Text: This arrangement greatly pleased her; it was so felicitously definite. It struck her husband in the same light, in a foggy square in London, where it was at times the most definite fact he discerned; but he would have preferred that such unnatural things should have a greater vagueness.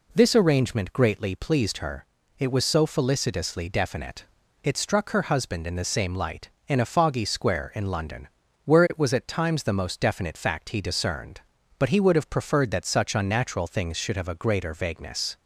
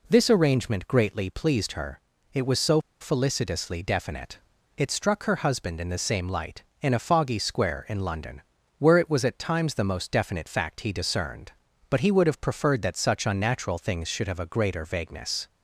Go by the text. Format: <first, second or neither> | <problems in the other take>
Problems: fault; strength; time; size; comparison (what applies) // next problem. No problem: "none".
first | pauses between "so" and "felicitously"; slight; at 2.8 s; 0.19 s long